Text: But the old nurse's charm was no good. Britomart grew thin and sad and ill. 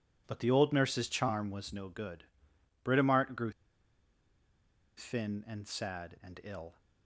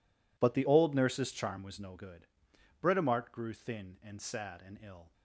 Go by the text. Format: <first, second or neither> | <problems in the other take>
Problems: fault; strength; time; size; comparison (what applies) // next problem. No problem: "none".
second | pauses between "grew" and "thin"; strong; at 3.5 s; 1.4 s long